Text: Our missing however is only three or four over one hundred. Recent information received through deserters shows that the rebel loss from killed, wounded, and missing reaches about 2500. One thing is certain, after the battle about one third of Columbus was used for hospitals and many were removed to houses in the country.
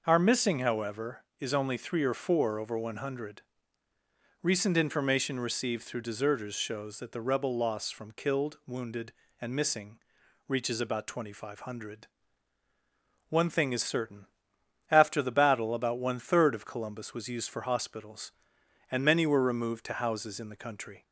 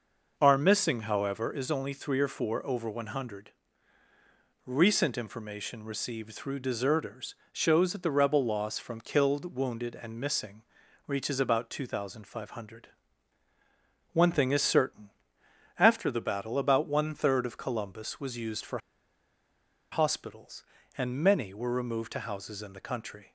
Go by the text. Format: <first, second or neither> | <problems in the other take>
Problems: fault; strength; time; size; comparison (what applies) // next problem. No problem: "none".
first | pauses between "deserters" and "shows"; slight; at 7.3 s; 0.18 s long // pauses between "missing" and "reaches"; noticeable; at 10.6 s; 0.46 s long; noticeable in the first // pauses between "for" and "hospitals"; at 18.7 s; 1.1 s long